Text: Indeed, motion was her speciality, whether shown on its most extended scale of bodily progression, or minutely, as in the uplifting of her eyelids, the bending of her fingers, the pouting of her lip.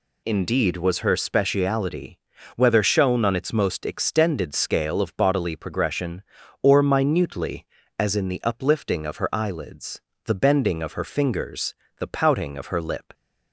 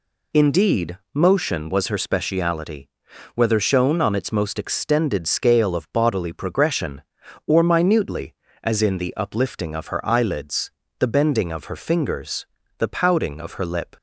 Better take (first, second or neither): second